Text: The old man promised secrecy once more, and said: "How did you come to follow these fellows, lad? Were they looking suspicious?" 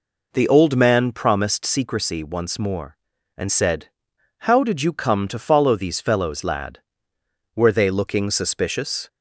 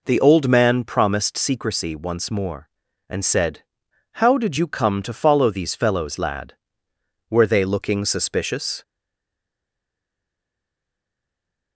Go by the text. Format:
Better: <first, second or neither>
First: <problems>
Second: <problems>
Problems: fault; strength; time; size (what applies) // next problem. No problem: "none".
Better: first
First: none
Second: stays silent after the last word; strong; from 8.8 s on; 2.9 s long